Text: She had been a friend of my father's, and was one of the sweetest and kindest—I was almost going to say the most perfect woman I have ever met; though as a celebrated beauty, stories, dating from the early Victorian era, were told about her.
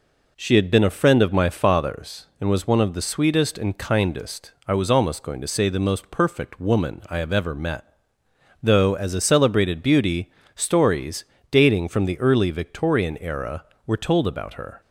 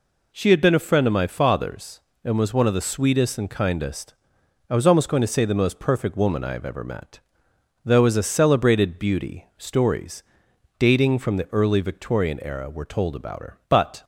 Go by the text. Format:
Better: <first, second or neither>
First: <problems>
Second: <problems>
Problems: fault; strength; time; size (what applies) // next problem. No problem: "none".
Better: first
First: none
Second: goes on to say "But"; slight; from 13.6 s on; 0.36 s long